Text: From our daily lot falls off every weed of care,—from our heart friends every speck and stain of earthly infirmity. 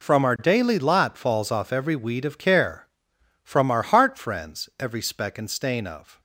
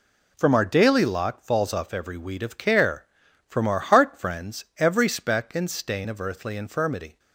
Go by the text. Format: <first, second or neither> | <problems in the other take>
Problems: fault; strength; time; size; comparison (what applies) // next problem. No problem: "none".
second | stops before "earthly infirmity"; at 6.1 s